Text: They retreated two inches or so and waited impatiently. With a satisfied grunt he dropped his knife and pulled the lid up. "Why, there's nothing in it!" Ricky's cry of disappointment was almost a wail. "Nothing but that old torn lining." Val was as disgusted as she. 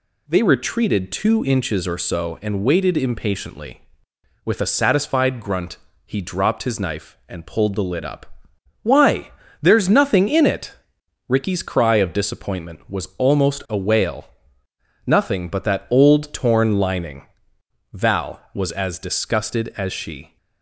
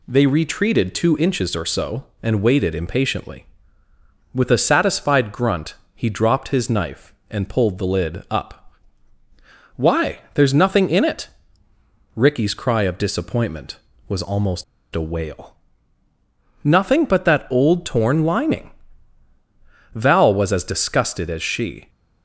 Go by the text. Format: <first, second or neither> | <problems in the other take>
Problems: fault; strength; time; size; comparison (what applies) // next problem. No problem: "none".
first | pauses between "grunt" and "he"; slight; at 5.7 s; 0.20 s long; slight in the first // pauses between "almost" and "a"; slight; at 14.6 s; 0.31 s long